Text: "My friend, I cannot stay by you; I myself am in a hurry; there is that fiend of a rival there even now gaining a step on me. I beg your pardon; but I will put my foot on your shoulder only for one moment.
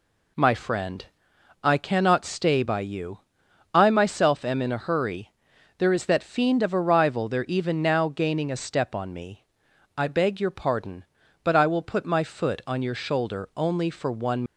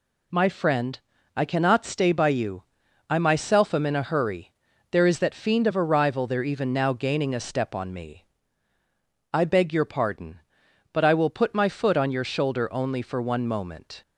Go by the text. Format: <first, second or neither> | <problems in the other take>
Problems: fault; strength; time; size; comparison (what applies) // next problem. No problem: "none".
second | stops before "moment"; at 14.4 s